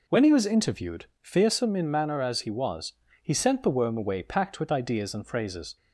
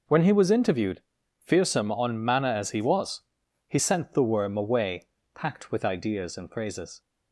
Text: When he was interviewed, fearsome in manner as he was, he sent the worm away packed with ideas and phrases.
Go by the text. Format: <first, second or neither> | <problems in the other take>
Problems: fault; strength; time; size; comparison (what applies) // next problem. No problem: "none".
first | says "on" for "in"; at 1.9 s // pauses between "away" and "packed"; slight; at 5.0 s; 0.26 s long